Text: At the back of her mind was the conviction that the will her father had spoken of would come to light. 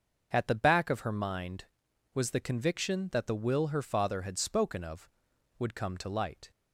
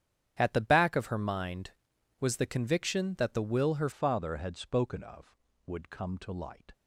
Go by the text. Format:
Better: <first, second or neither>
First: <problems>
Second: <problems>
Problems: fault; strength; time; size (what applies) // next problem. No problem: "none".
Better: first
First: starts louder than the rest; until 1.3 s; 6.5 dB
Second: starts louder than the rest; strong; until 1.4 s; 9.5 dB // changes voice at "father"; from 3.9 s on; 2.8 s long